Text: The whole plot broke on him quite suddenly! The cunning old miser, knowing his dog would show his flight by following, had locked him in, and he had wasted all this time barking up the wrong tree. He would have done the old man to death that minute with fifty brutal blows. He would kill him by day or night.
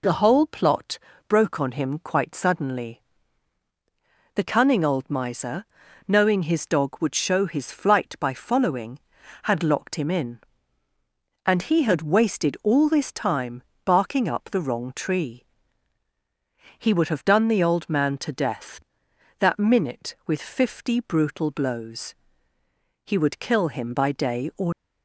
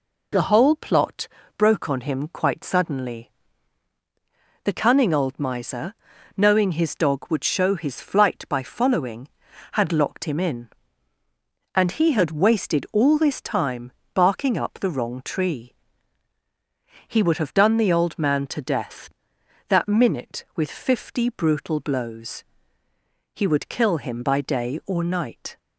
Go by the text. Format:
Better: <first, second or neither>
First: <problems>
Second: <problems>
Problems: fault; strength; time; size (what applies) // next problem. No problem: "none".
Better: second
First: pauses between "plot" and "broke"; slight; at 0.9 s; 0.30 s long // pauses between "time" and "barking"; slight; at 13.6 s; 0.24 s long // stops before "night"; at 24.7 s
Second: pauses between "plot" and "broke"; slight; at 1.2 s; 0.30 s long // pauses between "time" and "barking"; slight; at 13.9 s; 0.24 s long